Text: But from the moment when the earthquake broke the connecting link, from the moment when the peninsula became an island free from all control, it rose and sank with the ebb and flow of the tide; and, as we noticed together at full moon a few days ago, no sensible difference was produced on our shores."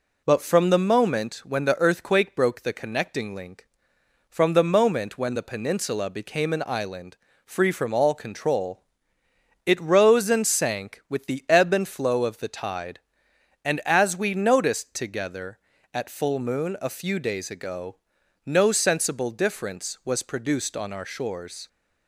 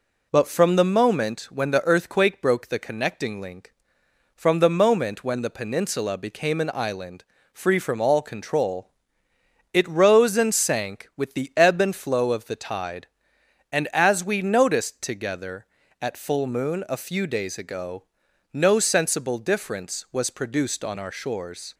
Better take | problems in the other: neither | pauses between "island" and "free"; slight; the same in both

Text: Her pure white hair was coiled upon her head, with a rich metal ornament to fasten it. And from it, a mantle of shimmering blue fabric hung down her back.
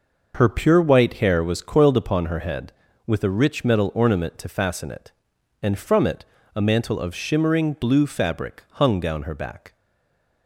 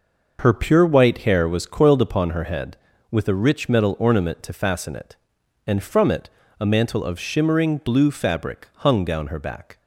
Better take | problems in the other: second | stays silent after the last word; slight; from 9.7 s on; 0.7 s long

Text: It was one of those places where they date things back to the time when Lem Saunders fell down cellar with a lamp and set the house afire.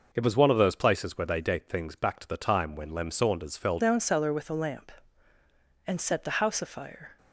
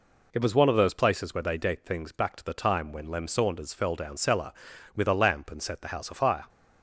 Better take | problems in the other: second | changes voice at "down"; from 3.7 s on; 3.4 s long

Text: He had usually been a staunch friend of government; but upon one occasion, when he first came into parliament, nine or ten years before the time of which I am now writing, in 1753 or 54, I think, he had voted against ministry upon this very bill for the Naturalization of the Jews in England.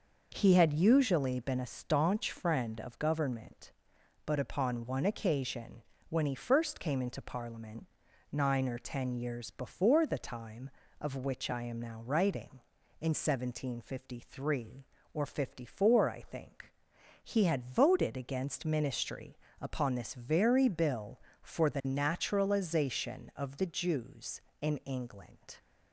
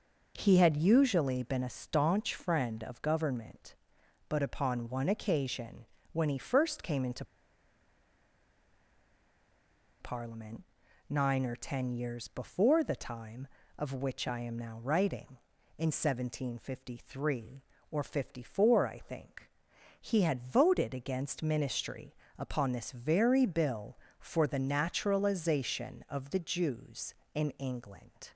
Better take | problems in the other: first | pauses between "into" and "parliament"; strong; at 7.2 s; 2.7 s long // pauses between "ministry" and "upon"; slight; at 22.1 s; 0.24 s long; slight in the first

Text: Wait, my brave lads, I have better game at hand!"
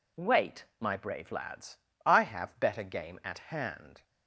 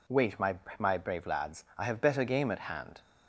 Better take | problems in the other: first | says "my" twice; at 0.7 s

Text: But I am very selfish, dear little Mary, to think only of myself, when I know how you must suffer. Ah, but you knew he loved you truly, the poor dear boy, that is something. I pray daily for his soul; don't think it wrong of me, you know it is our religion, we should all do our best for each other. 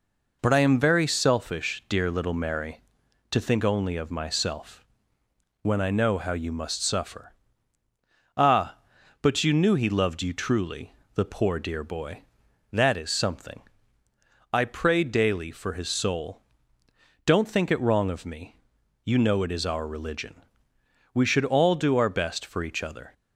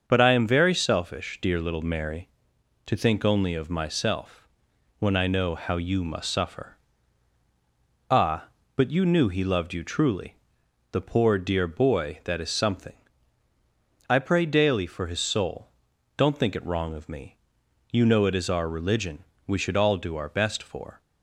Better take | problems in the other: first | starts louder than the rest; until 1.0 s; 6.5 dB // stops before "each other"; at 21.0 s

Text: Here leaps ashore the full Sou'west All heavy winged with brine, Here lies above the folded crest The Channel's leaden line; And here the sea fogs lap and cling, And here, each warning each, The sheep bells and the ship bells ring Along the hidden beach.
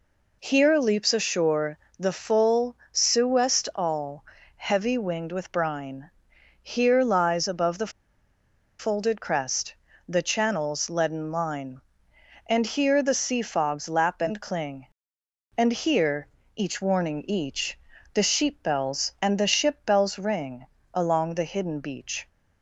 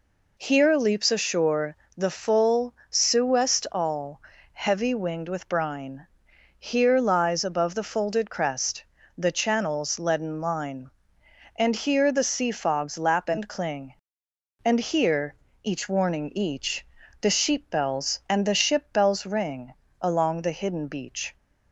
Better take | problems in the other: second | pauses between "ashore" and "the"; slight; at 1.7 s; 0.22 s long; slight in the second // pauses between "full" and "Sou'west"; slight; at 2.7 s; 0.16 s long; slight in the second // pauses between "All" and "heavy"; slight; at 4.2 s; 0.32 s long; slight in the second // pauses between "the" and "folded"; noticeable; at 7.9 s; 0.88 s long // pauses between "crest" and "The"; slight; at 9.7 s; 0.34 s long; slight in the second // pauses between "ring" and "Along"; slight; at 20.6 s; 0.28 s long; slight in the second

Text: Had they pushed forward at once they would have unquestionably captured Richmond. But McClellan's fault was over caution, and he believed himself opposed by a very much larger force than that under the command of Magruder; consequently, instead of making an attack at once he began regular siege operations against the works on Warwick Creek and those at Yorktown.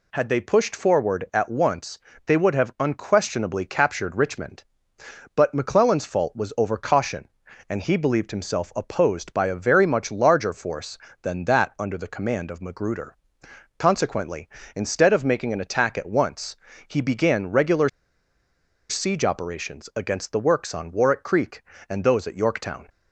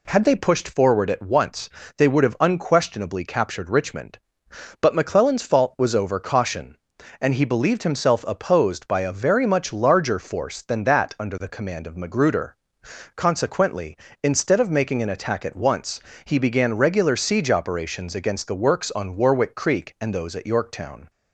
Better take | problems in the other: second | pauses between "once" and "they"; slight; at 1.9 s; 0.30 s long; slight in the second // pauses between "once" and "he"; slight; at 16.5 s; 0.32 s long; slight in the second // pauses between "regular" and "siege"; at 17.8 s; 1.0 s long

